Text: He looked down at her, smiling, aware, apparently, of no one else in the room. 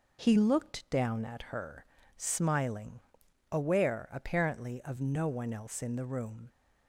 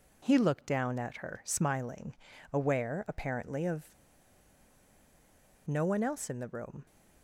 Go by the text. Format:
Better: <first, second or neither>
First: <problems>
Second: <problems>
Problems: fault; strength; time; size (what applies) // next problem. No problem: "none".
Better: first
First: none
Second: pauses between "of" and "no"; strong; at 3.9 s; 1.7 s long